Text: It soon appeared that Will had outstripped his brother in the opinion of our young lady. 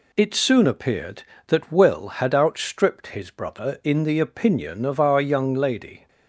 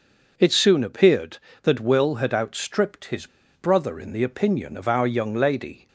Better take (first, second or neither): first